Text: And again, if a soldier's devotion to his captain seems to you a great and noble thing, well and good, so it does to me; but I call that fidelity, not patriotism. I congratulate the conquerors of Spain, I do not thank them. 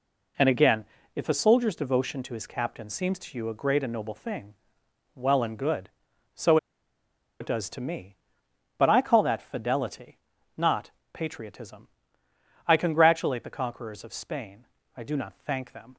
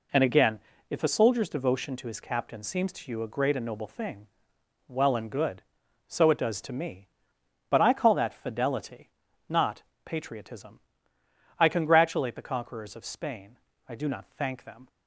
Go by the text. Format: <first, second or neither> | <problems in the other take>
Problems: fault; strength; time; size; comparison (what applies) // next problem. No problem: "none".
second | pauses between "so" and "it"; noticeable; at 6.5 s; 0.83 s long // pauses between "not" and "patriotism"; slight; at 10.8 s; 0.24 s long; slight in the second